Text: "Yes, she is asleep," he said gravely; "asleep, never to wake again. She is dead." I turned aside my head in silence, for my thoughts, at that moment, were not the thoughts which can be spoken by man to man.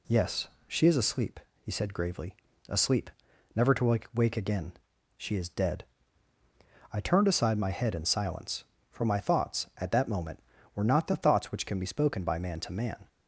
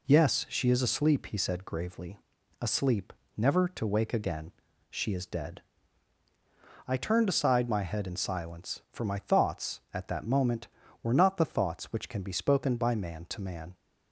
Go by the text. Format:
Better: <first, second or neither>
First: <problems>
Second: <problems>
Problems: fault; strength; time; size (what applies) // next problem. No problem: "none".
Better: second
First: says "wake" twice; at 4.1 s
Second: none